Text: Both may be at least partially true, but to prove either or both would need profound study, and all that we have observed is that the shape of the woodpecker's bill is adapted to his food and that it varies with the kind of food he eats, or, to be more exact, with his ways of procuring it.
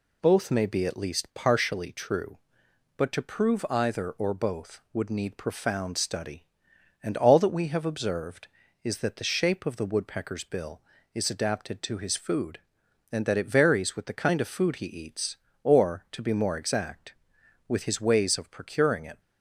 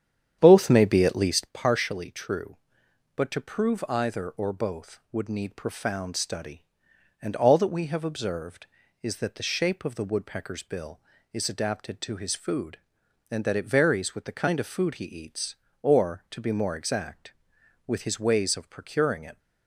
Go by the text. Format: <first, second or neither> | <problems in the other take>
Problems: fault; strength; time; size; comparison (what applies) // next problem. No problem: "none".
first | starts louder than the rest; strong; until 1.6 s; 9 dB